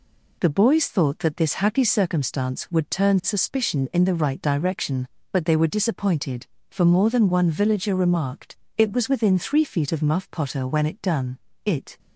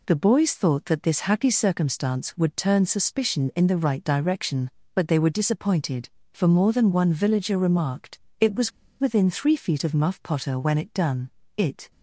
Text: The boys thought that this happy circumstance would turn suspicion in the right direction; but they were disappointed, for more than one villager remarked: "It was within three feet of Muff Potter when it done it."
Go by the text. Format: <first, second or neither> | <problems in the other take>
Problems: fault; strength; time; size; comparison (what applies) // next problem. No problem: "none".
first | pauses between "was" and "within"; slight; at 8.7 s; 0.29 s long // pauses between "done" and "it"; slight; at 11.3 s; 0.26 s long; slight in the first